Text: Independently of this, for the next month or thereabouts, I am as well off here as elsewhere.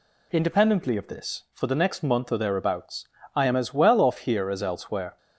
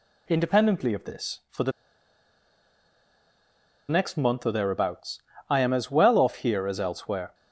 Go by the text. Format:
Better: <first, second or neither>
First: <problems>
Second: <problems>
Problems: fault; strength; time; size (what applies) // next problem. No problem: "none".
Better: first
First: none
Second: pauses between "the" and "next"; strong; at 1.7 s; 2.1 s long